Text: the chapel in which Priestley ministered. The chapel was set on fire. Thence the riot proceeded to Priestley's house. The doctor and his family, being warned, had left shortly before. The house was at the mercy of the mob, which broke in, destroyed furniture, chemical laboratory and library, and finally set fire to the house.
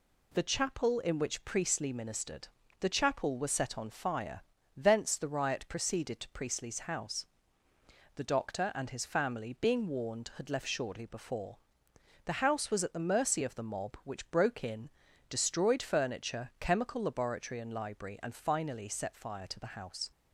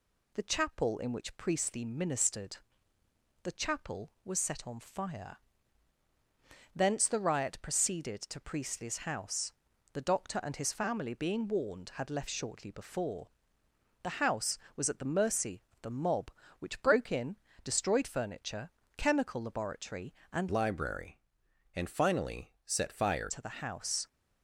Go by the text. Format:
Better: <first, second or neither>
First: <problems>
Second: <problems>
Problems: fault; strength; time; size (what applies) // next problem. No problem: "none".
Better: first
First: none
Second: changes voice from "library" to "fire"; from 20.4 to 23.2 s; 2.8 s long